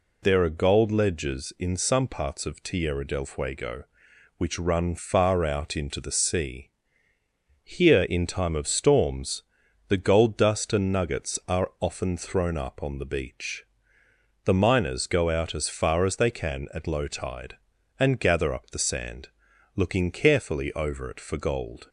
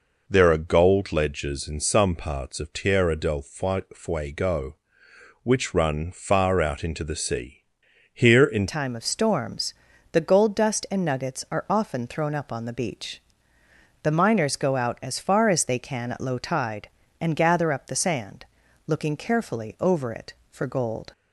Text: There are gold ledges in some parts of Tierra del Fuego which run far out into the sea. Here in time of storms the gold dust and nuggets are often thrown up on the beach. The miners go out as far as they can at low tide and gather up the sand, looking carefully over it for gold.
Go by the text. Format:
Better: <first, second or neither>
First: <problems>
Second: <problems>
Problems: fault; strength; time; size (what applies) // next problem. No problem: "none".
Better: first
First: pauses between "storms" and "the"; noticeable; at 9.4 s; 0.48 s long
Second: changes voice at "time"; from 8.6 s on; 12.5 s long // pauses between "storms" and "the"; at 9.7 s; 0.40 s long